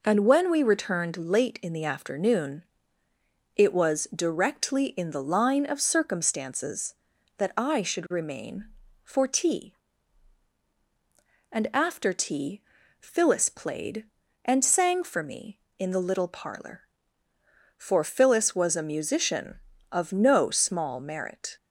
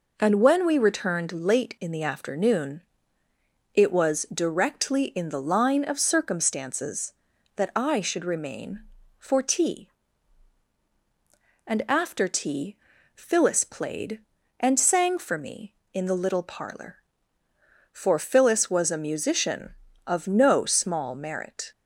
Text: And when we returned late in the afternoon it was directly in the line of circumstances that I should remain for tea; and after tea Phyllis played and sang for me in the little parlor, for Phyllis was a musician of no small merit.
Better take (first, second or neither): neither